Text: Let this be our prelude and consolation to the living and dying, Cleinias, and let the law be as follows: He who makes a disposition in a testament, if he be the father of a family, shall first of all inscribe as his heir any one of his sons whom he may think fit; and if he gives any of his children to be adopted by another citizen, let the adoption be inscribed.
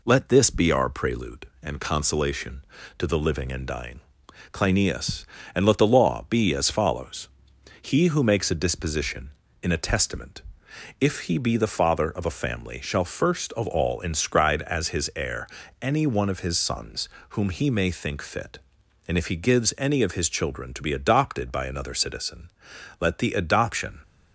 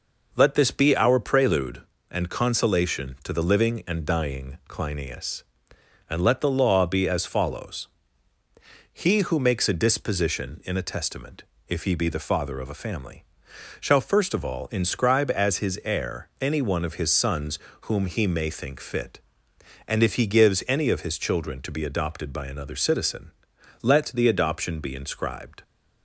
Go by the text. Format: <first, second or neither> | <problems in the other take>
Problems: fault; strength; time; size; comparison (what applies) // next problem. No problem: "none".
second | pauses between "heir" and "any"; slight; at 15.4 s; 0.34 s long // pauses between "sons" and "whom"; slight; at 17.0 s; 0.30 s long; slight in the second // stops before "be inscribed"; at 24.0 s